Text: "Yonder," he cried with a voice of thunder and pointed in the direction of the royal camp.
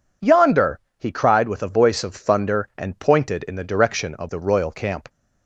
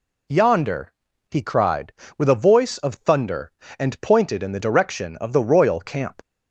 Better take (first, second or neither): neither